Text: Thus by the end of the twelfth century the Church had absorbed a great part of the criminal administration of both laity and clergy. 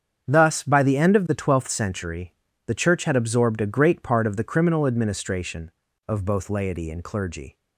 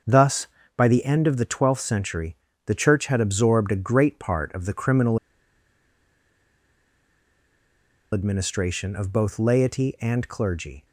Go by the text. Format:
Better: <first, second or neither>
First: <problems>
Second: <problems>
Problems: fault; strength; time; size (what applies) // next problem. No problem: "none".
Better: first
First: starts louder than the rest; strong; until 1.3 s; 7.5 dB // pauses between "century" and "the"; slight; at 2.3 s; 0.32 s long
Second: starts louder than the rest; until 1.3 s; 6.5 dB // pauses between "century" and "the"; slight; at 2.3 s; 0.30 s long // pauses between "criminal" and "administration"; strong; at 5.1 s; 2.9 s long